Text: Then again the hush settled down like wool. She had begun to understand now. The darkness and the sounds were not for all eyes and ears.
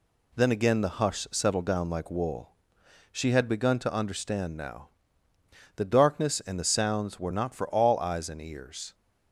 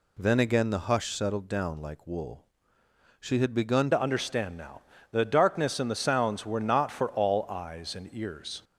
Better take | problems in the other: first | changes voice at "to"; from 3.9 s on; 4.7 s long

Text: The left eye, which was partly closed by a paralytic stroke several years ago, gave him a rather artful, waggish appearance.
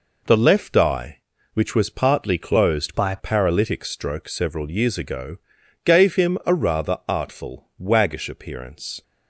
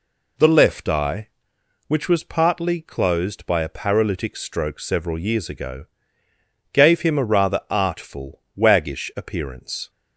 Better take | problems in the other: second | changes voice from "by" to "a"; from 2.9 to 3.1 s; 0.2 s long

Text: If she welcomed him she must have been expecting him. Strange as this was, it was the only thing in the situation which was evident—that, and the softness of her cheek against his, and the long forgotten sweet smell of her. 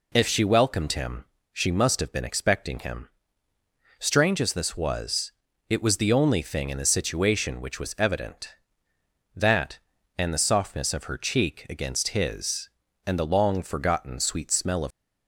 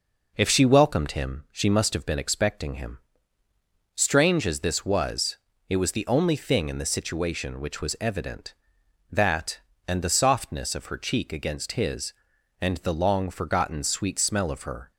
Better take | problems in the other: second | pauses between "him" and "she"; slight; at 1.2 s; 0.28 s long // stops before "her"; at 14.9 s

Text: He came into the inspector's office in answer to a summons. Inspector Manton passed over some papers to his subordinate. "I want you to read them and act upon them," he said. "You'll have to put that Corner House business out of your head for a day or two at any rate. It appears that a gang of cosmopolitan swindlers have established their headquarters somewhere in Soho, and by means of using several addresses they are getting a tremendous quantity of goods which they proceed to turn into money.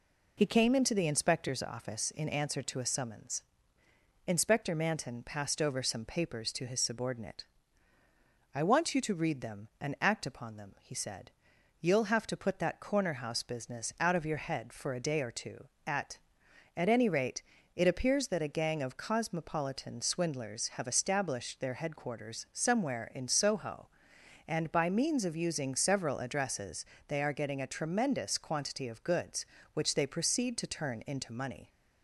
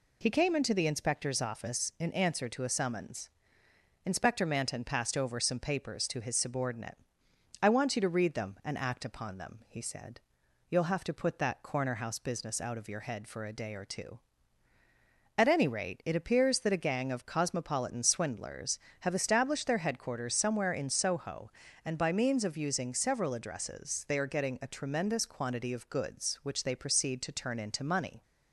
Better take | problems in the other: second | says "at" twice; at 16.7 s // pauses between "addresses" and "they"; slight; at 26.8 s; 0.26 s long

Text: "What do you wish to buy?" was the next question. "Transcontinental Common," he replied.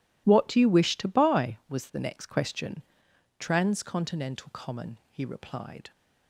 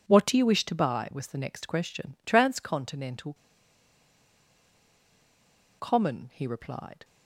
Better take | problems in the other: first | pauses between "Transcontinental" and "Common"; strong; at 3.3 s; 2.4 s long

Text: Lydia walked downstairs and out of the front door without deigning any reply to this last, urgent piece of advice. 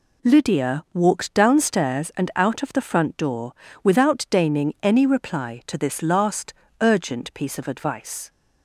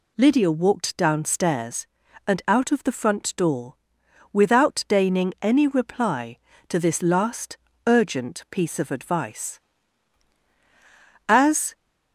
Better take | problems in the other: first | pauses between "door" and "without"; noticeable; at 3.7 s; 0.58 s long; slight in the first // goes on to say "As"; slight; from 11.2 s on; 0.46 s long

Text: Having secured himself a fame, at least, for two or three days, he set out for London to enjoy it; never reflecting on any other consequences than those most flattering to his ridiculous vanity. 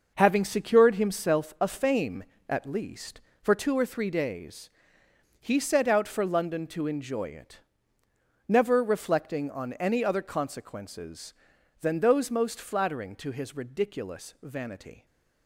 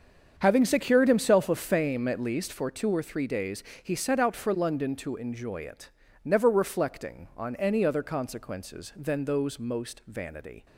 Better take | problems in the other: first | starts louder than the rest; strong; until 1.3 s; 7 dB // skips "flattering to his ridiculous"; at 10.0 s

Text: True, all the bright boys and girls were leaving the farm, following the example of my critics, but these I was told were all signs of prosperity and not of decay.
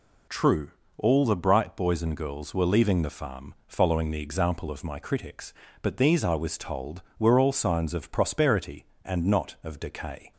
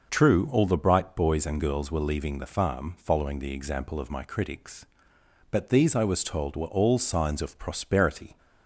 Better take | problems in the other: first | starts louder than the rest; noticeable; until 1.1 s; 6 dB // stops before "and not of decay"; at 8.3 s

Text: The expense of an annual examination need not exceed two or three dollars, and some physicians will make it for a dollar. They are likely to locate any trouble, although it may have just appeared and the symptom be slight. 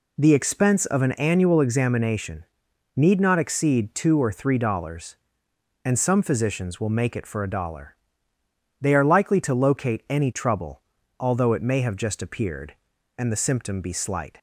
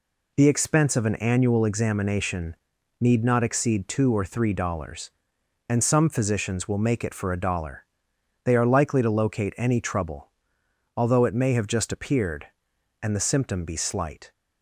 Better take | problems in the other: neither | pauses between "examination" and "need"; the same in both

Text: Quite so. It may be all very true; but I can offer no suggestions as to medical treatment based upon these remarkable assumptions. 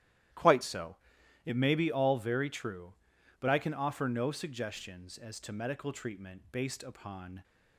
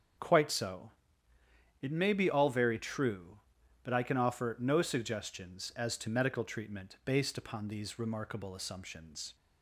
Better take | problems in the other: second | starts louder than the rest; strong; until 1.8 s; 13.5 dB; also in the second // stops before "these remarkable assumptions"; at 7.4 s

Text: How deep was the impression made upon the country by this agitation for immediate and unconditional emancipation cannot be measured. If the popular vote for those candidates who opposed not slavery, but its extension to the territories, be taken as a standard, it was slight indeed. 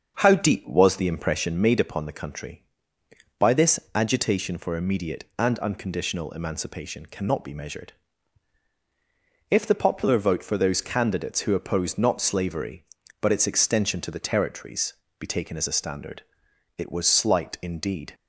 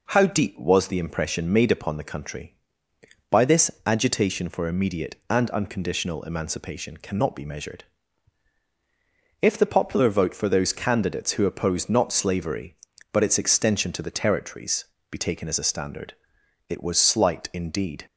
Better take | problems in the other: second | starts louder than the rest; until 1.6 s; 6.5 dB

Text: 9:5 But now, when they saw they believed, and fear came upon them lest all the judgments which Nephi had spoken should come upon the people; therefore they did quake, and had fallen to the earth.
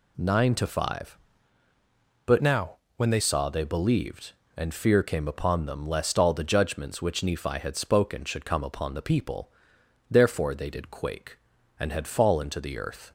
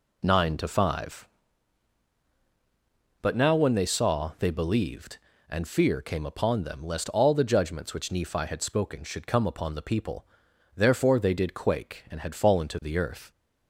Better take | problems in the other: second | changes voice from "now" to "they"; from 2.4 to 3.1 s; 0.7 s long

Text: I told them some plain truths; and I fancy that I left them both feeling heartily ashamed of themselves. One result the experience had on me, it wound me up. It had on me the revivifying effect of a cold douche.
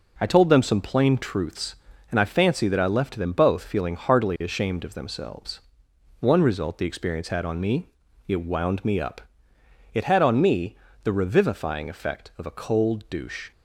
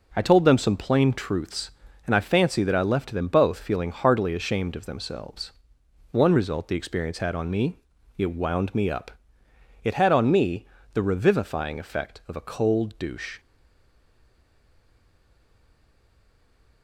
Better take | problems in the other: first | pauses between "me" and "the"; slight; at 10.6 s; 0.28 s long; slight in the first // stays silent after the last word; strong; from 13.3 s on; 3.5 s long

